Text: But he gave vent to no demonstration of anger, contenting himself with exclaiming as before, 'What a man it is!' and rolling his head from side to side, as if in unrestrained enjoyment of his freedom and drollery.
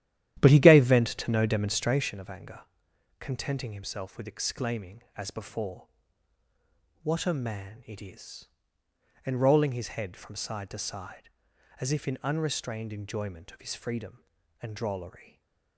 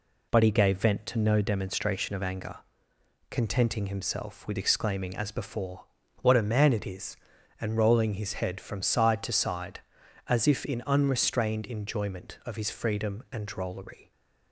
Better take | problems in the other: second | starts louder than the rest; strong; until 2.1 s; 11.5 dB // stays silent after the last word; slight; from 15.1 s on; 0.6 s long

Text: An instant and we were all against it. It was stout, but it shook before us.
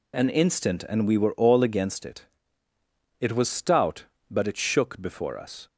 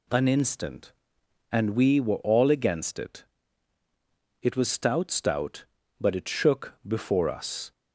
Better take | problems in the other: first | says "stout" twice; at 5.1 s

